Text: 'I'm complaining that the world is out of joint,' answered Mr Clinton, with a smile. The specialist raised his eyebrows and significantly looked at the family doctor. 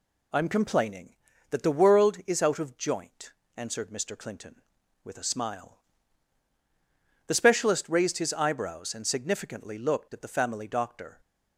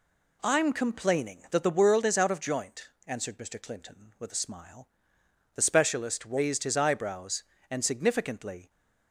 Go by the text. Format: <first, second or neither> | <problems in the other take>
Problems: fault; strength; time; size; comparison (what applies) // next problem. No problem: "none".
first | stops before "looked at the family doctor"; at 8.6 s